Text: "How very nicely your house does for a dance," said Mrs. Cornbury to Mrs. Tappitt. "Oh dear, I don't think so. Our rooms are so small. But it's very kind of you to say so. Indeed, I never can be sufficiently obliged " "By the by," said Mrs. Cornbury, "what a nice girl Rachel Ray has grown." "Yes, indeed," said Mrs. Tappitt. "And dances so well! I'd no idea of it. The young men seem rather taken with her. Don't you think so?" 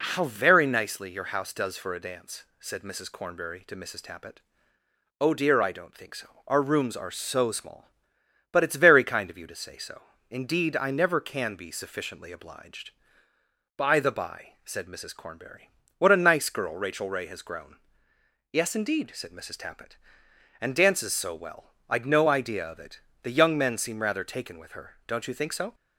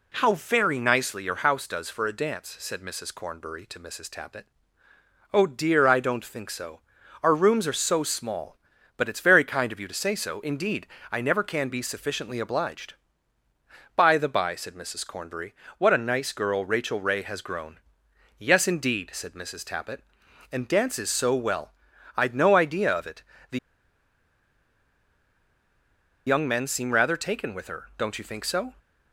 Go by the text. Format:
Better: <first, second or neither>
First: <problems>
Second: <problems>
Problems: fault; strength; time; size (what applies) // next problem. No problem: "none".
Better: first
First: none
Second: pauses between "The" and "young"; strong; at 23.5 s; 2.6 s long